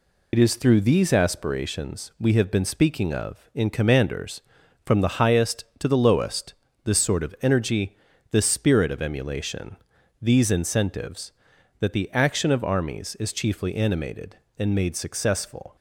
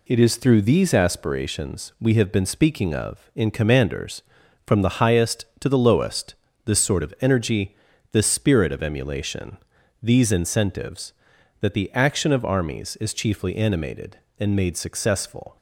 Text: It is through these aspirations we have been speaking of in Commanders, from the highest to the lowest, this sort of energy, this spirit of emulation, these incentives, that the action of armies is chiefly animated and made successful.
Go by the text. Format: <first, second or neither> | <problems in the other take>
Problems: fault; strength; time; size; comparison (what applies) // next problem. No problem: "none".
second | loses the start of "It"; at 0.3 s; 60 ms